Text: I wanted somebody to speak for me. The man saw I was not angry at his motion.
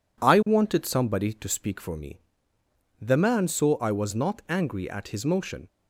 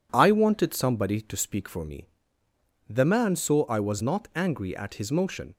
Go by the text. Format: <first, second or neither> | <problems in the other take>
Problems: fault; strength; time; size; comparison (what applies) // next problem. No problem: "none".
neither | none